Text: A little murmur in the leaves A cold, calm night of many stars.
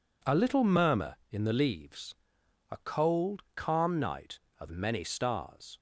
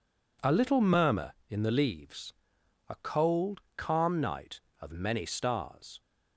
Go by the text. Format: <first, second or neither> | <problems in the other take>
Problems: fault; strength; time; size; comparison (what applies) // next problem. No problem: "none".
neither | pauses between "leaves" and "A"; noticeable; the same in both